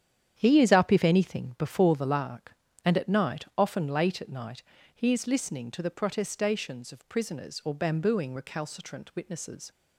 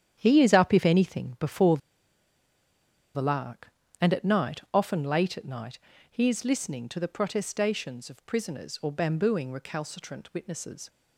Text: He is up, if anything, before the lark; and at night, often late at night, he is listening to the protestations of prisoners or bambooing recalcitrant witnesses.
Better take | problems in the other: first | starts louder than the rest; strong; until 1.2 s; 9.5 dB; strong in the first // pauses between "before" and "the"; strong; at 1.7 s; 1.3 s long

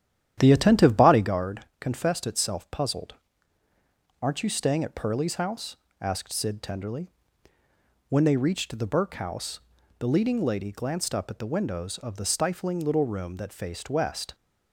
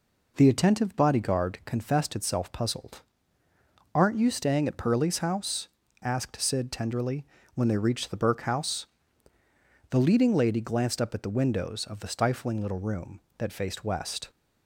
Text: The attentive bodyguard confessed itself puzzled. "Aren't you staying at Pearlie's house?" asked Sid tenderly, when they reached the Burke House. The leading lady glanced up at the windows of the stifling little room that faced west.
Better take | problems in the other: second | starts louder than the rest; strong; until 1.4 s; 10.5 dB // pauses between "bodyguard" and "confessed"; slight; at 1.6 s; 0.16 s long

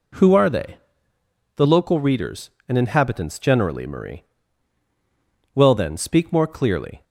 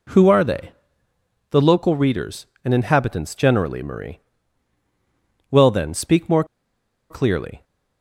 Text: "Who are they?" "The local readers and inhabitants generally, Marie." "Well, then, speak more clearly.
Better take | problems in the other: first | pauses between "more" and "clearly"; noticeable; at 6.4 s; 0.66 s long

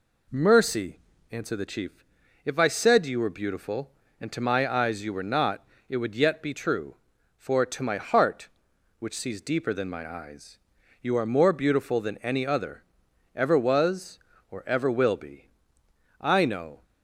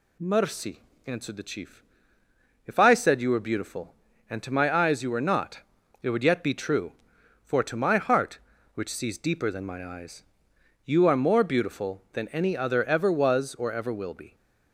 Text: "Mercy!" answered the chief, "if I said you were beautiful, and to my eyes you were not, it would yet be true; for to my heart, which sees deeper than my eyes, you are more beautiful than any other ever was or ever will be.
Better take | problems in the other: second | pauses between "other" and "ever"; noticeable; at 12.8 s; 0.52 s long // goes on to say "I know"; noticeable; from 16.2 s on; 0.62 s long

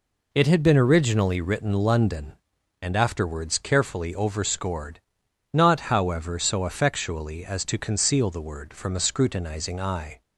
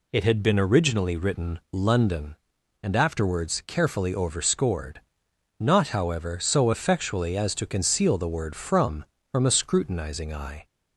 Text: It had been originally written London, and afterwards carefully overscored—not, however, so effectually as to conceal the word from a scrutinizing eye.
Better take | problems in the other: first | says "from" twice; at 9.3 s

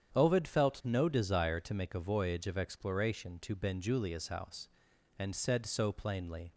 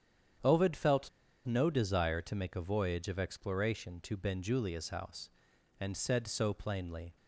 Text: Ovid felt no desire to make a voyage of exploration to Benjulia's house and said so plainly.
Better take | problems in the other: first | starts louder than the rest; strong; until 1.8 s; 8.5 dB; strong in the first // pauses between "felt" and "no"; at 1.0 s; 0.38 s long

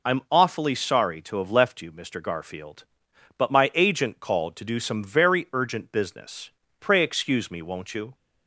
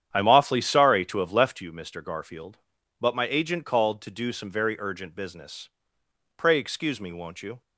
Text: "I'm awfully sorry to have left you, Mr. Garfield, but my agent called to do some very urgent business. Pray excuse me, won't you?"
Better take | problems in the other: first | starts louder than the rest; strong; until 1.7 s; 9.5 dB

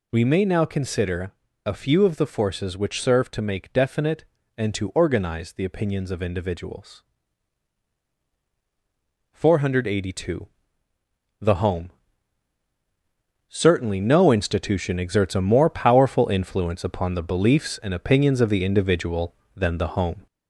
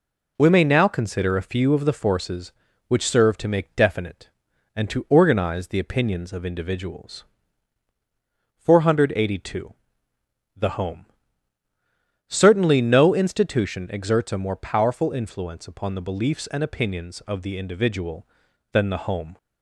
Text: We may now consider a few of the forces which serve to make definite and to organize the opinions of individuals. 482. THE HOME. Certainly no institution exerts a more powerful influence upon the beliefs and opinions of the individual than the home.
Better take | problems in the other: second | gets louder; slight; throughout; 2.5 dB // pauses between "consider" and "a"; slight; at 1.3 s; 0.32 s long

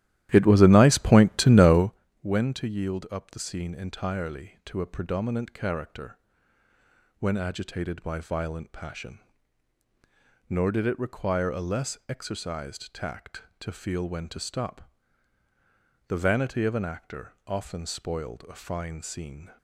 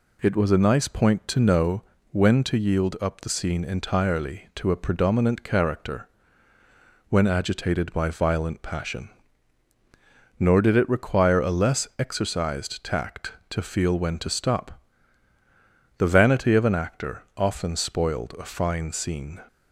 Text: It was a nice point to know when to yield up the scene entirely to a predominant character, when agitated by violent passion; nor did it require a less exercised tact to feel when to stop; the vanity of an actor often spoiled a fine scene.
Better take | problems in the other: second | starts louder than the rest; strong; until 2.0 s; 13.5 dB // pauses between "know" and "when"; slight; at 1.9 s; 0.30 s long; slight in the second // pauses between "actor" and "often"; slight; at 17.3 s; 0.16 s long; slight in the second

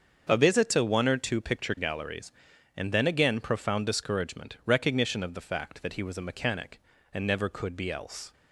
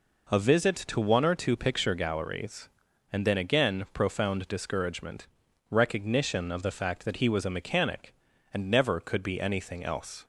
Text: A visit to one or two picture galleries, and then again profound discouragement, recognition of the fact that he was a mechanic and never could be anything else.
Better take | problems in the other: second | starts louder than the rest; until 1.3 s; 7 dB // skips "anything"; at 7.9 s

